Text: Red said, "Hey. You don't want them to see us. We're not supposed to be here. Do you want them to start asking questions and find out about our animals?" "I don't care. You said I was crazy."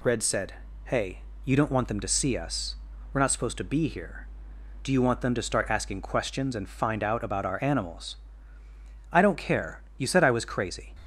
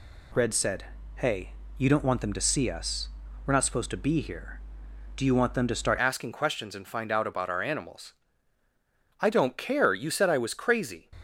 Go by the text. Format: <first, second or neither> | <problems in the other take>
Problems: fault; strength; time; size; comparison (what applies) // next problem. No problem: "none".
first | changes voice at "asking"; from 5.9 s on; 5.2 s long